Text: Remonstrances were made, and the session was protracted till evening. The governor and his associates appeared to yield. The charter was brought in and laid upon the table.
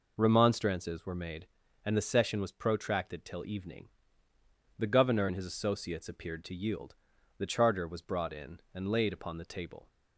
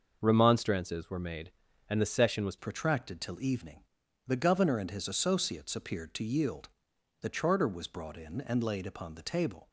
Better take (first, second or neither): first